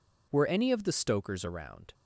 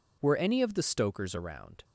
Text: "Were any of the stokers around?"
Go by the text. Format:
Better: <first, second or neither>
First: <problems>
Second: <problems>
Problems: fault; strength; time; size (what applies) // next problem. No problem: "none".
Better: neither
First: none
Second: none